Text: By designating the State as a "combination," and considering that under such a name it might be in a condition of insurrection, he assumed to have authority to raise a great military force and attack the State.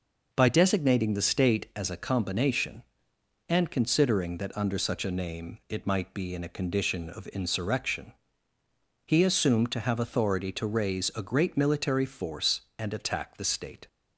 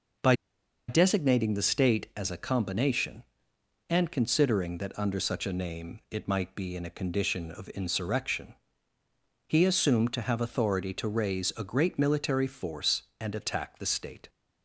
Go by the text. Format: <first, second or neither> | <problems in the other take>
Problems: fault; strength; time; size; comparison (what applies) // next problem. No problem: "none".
first | pauses between "By" and "designating"; noticeable; at 0.3 s; 0.54 s long